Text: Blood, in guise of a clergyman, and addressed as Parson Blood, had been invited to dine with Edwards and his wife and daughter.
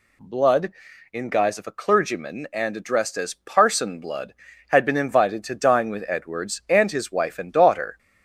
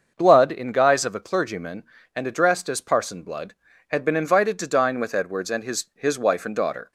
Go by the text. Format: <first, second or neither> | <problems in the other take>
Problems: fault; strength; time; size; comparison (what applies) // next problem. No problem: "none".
first | starts louder than the rest; until 1.1 s; 6.5 dB // says "his" twice; at 5.9 s